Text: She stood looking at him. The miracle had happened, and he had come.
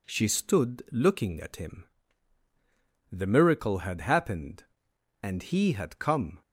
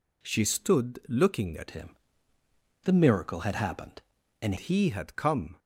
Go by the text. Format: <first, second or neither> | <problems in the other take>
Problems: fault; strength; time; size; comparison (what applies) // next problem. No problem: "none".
first | changes voice from "him" to "and"; from 1.7 to 4.5 s; 2.8 s long